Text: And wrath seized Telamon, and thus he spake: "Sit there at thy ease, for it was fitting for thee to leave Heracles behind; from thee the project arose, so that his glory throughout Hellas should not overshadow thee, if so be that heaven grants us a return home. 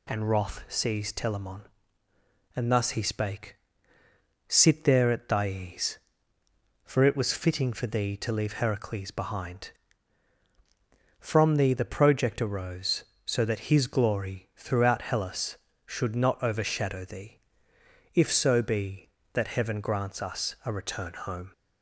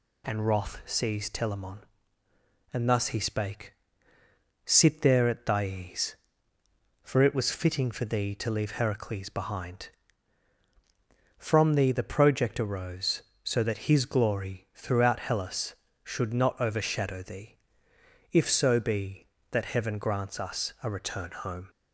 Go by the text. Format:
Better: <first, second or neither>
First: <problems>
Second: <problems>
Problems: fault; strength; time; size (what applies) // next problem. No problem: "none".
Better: neither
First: none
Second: none